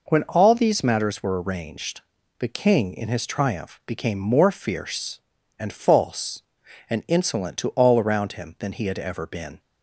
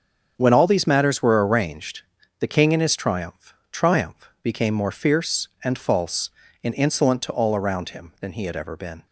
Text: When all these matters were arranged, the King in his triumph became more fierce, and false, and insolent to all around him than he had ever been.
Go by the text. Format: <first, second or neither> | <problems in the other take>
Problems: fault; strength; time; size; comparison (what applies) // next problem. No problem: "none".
first | starts louder than the rest; strong; until 1.3 s; 7 dB // says "triumph" twice; at 3.7 s